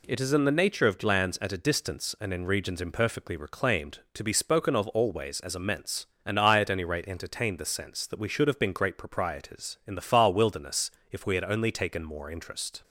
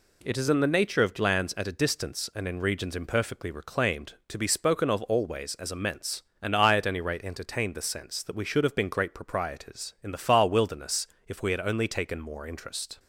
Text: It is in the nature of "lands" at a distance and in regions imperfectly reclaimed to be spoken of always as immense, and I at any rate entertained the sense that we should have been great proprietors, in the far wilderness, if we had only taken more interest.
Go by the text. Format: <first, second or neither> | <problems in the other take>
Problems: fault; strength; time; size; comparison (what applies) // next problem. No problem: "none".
neither | none